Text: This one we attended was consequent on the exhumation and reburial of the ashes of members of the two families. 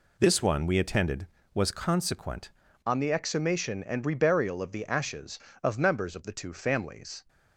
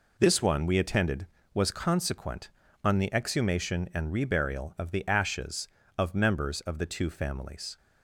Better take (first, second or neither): second